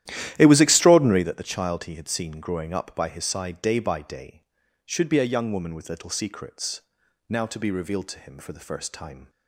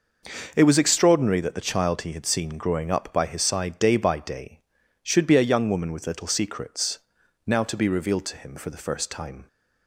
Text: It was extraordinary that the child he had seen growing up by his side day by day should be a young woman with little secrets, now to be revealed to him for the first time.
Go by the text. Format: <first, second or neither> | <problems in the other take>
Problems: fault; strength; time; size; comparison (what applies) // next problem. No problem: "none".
second | starts louder than the rest; strong; until 1.4 s; 12.5 dB